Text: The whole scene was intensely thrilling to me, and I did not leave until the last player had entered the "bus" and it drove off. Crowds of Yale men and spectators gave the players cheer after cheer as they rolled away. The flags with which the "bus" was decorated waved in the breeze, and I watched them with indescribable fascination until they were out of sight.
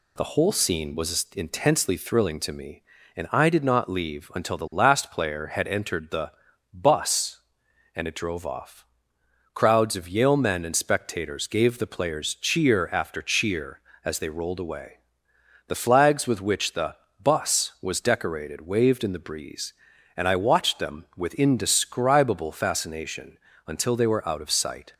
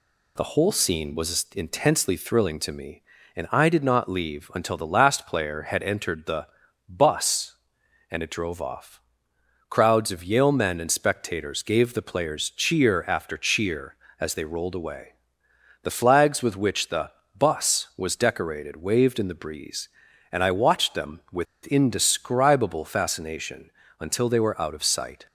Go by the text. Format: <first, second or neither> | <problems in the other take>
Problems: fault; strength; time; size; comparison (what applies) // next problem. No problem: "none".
first | pauses between "the" and "bus"; at 6.4 s; 0.40 s long; also in the first // pauses between "the" and "bus"; slight; at 17.1 s; 0.24 s long; slight in the first // pauses between "with" and "indescribable"; slight; at 21.4 s; 0.20 s long // pauses between "fascination" and "until"; slight; at 23.7 s; 0.26 s long; slight in the first